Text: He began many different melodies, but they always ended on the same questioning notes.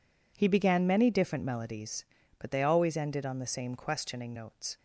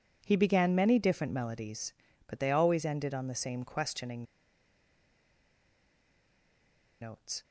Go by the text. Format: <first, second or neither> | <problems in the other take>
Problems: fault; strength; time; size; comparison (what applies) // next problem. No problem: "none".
first | pauses between "questioning" and "notes"; strong; at 4.2 s; 2.7 s long